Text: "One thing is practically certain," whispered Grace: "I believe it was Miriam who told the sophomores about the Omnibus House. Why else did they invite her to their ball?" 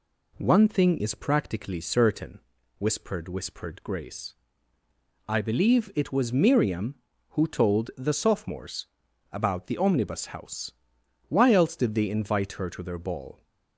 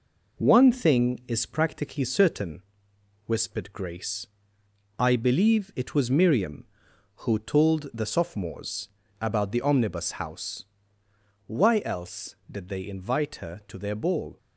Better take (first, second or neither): second